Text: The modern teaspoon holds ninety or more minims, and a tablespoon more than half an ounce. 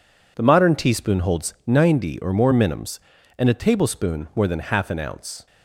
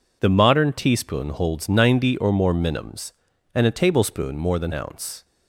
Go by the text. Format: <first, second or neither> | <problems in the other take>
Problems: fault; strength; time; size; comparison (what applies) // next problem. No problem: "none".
first | skips "half an"; at 4.7 s